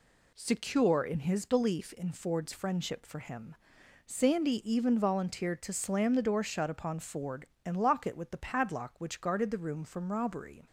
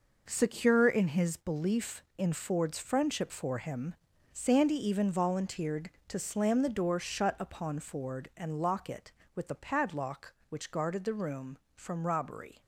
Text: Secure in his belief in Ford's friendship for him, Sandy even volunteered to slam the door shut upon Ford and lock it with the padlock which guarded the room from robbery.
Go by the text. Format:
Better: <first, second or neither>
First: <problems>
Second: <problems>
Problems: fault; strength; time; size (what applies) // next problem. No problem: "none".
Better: first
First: none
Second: gets quieter; strong; throughout; 8.5 dB